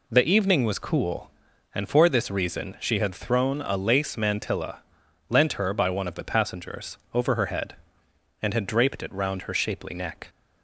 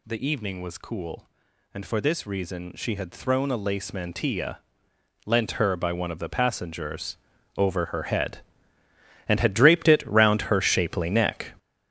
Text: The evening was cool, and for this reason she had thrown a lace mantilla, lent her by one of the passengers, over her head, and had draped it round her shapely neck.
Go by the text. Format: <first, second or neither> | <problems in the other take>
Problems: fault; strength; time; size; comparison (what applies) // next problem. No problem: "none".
first | gets louder; strong; throughout; 10 dB